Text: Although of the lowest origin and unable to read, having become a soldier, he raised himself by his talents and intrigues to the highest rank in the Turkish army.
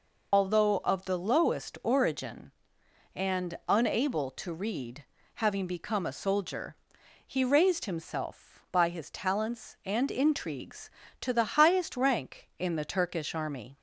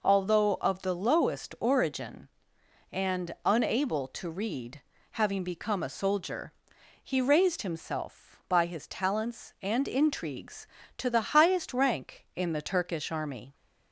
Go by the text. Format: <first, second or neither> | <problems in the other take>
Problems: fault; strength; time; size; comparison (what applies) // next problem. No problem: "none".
second | loses the start of "Although"; at 0.3 s; 75 ms